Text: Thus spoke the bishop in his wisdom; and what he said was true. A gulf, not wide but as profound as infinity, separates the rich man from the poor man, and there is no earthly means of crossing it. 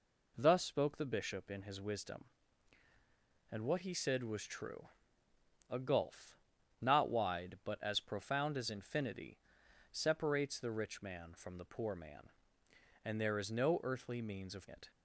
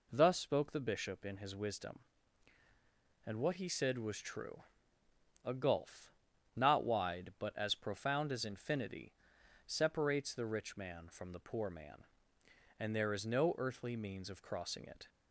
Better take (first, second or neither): second